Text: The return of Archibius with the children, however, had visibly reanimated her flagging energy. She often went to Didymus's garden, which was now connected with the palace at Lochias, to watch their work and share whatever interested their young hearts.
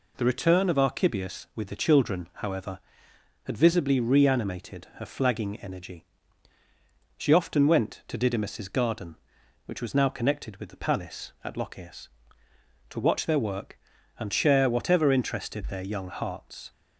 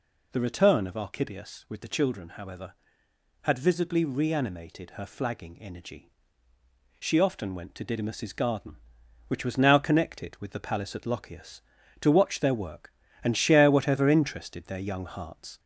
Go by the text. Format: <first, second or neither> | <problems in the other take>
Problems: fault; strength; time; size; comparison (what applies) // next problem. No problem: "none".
first | gets louder; slight; throughout; 2 dB